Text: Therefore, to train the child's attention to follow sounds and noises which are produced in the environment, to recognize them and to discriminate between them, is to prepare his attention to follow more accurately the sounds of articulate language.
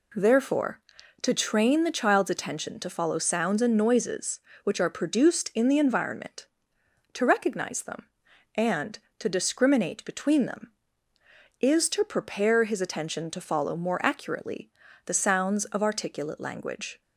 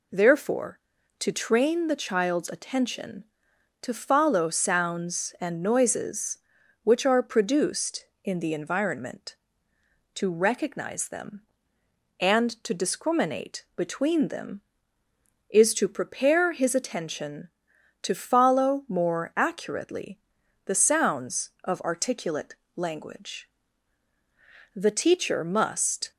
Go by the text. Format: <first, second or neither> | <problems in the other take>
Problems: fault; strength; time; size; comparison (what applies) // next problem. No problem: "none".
first | pauses between "accurately" and "the"; noticeable; at 20.1 s; 0.48 s long; slight in the first // pauses between "articulate" and "language"; slight; at 22.5 s; 0.34 s long // goes on to say "The teacher must"; from 24.7 s on; 1.3 s long